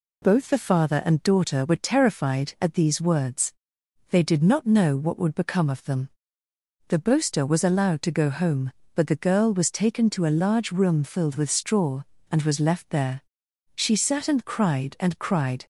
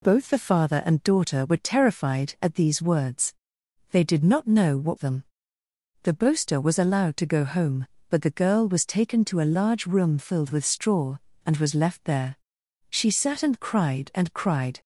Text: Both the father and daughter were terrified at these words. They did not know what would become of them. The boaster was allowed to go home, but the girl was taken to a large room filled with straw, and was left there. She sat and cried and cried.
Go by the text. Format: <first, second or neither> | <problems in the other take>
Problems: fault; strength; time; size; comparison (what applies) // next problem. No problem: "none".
first | skips "would become of"; at 4.9 s